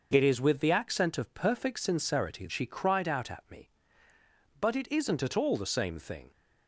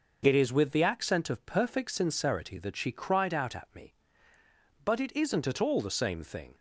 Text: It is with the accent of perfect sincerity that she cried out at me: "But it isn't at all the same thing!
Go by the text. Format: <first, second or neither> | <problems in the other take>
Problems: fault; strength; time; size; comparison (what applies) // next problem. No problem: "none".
second | skips "that"; at 2.4 s